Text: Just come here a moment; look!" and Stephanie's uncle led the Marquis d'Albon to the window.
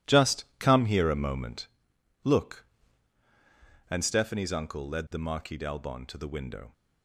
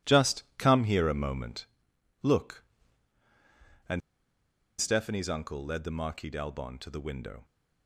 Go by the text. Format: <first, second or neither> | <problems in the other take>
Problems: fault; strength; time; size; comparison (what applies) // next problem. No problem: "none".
first | pauses between "and" and "Stephanie's"; noticeable; at 4.0 s; 0.80 s long